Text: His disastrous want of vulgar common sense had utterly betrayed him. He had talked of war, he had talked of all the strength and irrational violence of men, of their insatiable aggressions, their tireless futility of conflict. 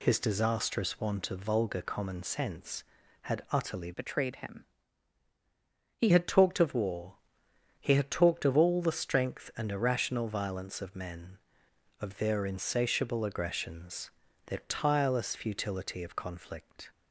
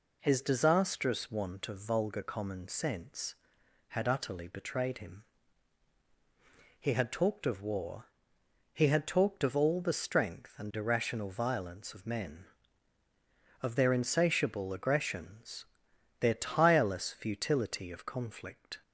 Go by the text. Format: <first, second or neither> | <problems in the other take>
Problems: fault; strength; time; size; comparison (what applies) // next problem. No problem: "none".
second | changes voice from "betrayed" to "He"; from 3.9 to 6.0 s; 2.1 s long